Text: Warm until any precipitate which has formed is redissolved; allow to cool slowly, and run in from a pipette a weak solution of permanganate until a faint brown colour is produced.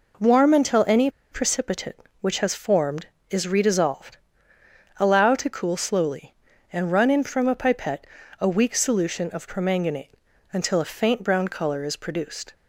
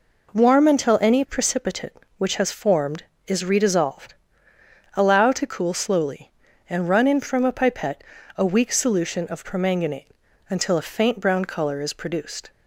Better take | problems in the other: second | pauses between "any" and "precipitate"; slight; at 1.0 s; 0.21 s long // pauses between "pipette" and "a"; slight; at 8.0 s; 0.36 s long; slight in the second // pauses between "permanganate" and "until"; at 10.1 s; 0.38 s long; also in the second

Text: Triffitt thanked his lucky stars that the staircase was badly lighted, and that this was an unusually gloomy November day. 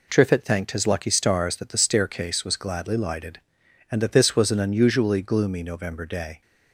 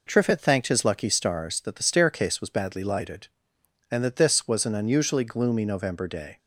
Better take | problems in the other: second | says "gladly" for "badly"; at 2.5 s

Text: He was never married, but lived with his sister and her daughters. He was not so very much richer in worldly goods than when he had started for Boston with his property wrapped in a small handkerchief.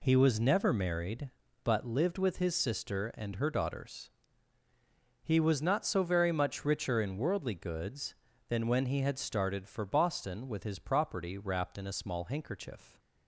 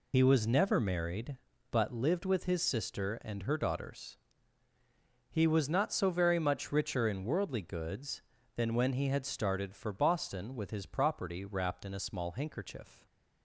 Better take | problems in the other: first | loses the start of "He"; at 0.1 s; 55 ms

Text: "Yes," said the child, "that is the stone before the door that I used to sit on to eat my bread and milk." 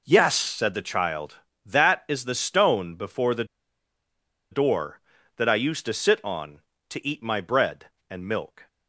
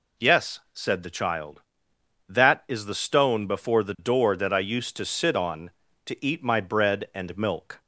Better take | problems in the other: second | pauses between "the" and "door"; at 3.4 s; 1.0 s long

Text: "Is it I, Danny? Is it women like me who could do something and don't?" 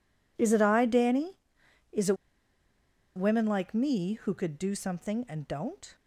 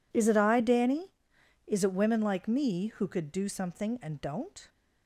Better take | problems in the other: second | pauses between "it" and "women"; at 2.1 s; 1.0 s long

